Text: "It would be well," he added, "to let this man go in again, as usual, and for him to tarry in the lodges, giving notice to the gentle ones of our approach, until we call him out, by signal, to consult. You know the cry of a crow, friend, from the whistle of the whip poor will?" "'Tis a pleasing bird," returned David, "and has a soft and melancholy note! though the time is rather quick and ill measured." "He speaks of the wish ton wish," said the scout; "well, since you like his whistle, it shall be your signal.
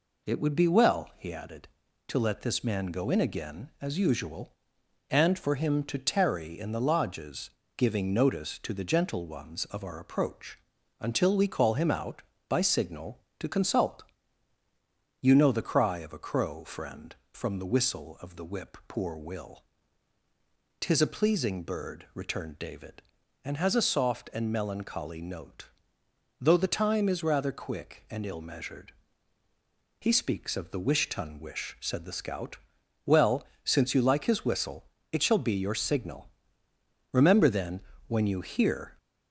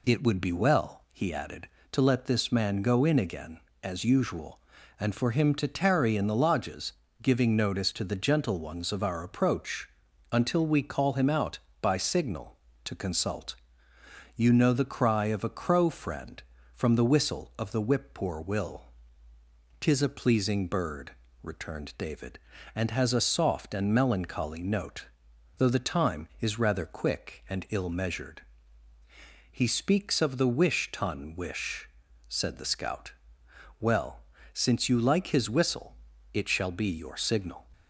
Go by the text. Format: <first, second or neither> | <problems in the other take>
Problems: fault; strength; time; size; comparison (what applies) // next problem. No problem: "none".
second | goes on to say "Remember then when you hear"; strong; from 37.1 s on; 1.8 s long